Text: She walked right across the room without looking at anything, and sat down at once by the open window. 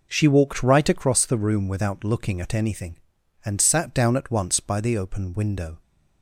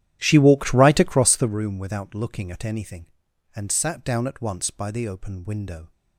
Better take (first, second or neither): first